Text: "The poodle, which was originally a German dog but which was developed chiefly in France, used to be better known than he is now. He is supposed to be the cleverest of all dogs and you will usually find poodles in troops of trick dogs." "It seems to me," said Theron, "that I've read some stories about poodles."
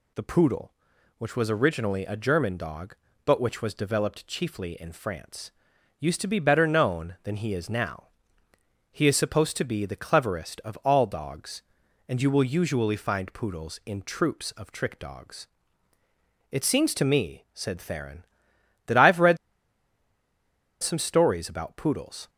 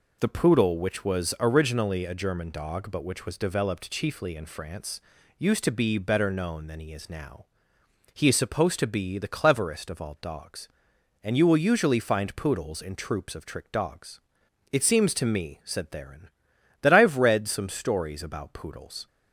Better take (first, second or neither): second